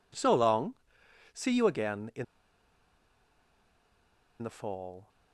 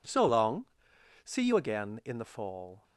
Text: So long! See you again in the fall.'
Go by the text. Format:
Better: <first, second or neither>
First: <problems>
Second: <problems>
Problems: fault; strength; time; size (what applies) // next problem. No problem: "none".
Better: second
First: pauses between "in" and "the"; strong; at 2.2 s; 2.1 s long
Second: none